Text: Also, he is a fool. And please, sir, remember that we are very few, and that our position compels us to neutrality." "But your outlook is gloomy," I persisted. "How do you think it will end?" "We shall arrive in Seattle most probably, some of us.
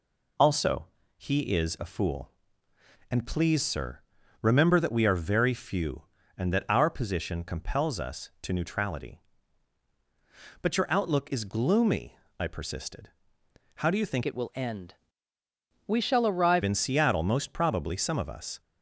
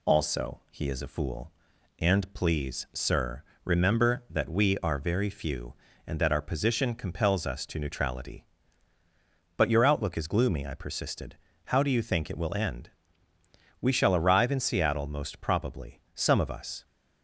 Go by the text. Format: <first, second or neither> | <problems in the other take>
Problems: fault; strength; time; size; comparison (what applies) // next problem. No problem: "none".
second | changes voice from "it" to "arrive"; from 14.2 to 16.6 s; 2.4 s long